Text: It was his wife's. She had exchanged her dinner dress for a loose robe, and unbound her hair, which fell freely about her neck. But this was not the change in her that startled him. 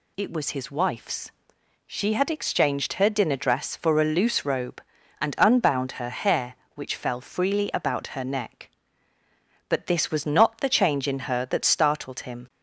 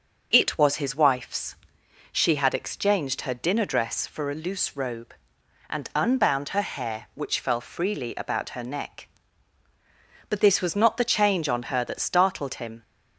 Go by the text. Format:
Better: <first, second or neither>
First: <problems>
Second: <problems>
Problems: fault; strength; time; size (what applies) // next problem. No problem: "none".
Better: first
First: none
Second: starts louder than the rest; until 1.3 s; 6.5 dB // says "on" for "in"; at 11.4 s